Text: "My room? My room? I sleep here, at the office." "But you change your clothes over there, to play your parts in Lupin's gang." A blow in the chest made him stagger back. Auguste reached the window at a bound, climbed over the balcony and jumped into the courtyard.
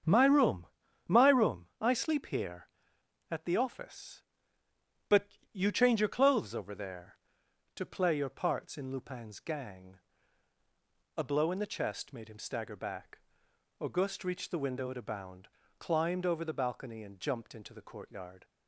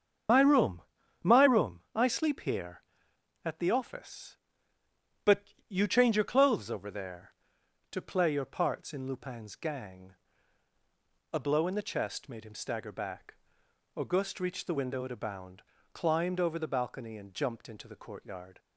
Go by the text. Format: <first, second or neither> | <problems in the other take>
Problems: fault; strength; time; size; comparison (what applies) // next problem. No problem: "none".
first | loses the start of "My"; at 0.2 s; 100 ms // starts louder than the rest; strong; until 1.7 s; 8 dB; strong in the first